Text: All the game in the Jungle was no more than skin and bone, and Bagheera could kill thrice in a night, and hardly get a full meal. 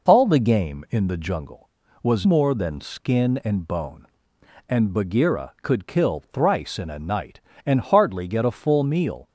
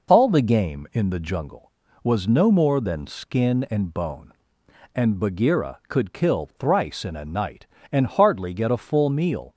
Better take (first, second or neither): second